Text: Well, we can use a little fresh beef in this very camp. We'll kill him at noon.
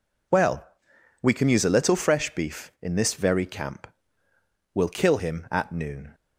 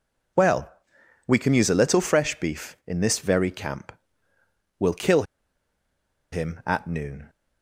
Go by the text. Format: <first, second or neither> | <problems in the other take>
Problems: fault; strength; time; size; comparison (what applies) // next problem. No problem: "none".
first | pauses between "kill" and "him"; at 5.2 s; 1.0 s long